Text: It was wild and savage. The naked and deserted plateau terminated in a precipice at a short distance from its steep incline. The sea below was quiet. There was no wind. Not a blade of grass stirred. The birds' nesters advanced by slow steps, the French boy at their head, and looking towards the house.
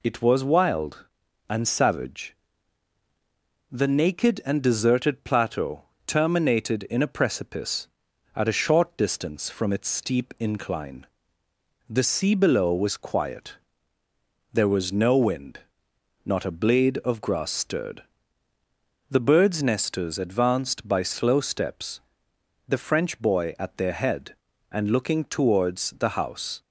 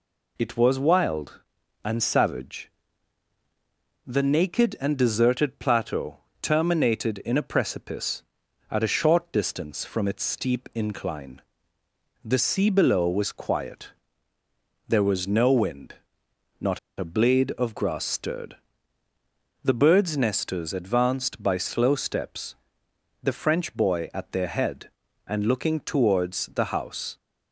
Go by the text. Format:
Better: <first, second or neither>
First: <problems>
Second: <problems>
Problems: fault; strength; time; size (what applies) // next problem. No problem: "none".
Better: first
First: pauses between "plateau" and "terminated"; slight; at 5.8 s; 0.24 s long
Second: pauses between "plateau" and "terminated"; slight; at 6.1 s; 0.24 s long // pauses between "Not" and "a"; slight; at 16.7 s; 0.19 s long